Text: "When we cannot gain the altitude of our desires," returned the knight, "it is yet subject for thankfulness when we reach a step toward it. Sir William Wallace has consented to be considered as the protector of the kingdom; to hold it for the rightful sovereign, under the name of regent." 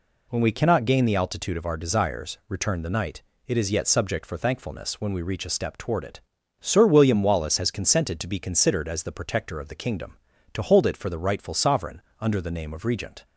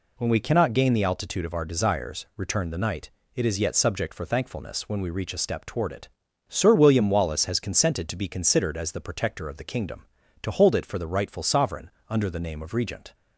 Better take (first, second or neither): neither